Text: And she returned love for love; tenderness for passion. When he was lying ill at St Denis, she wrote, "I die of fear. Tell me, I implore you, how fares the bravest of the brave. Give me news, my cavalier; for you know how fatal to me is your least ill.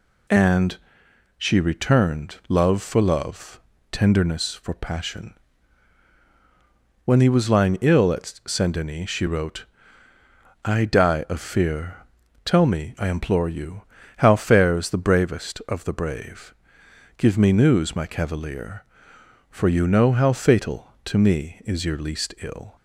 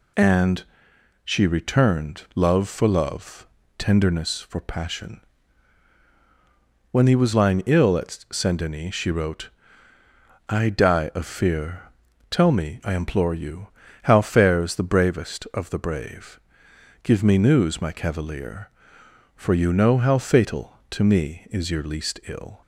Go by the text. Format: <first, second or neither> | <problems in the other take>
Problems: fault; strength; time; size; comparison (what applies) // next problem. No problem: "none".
neither | pauses between "And" and "she"; noticeable; the same in both